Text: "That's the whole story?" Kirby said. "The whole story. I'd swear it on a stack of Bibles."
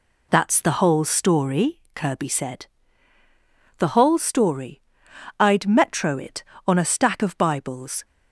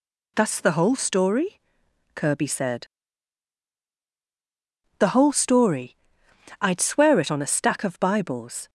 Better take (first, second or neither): second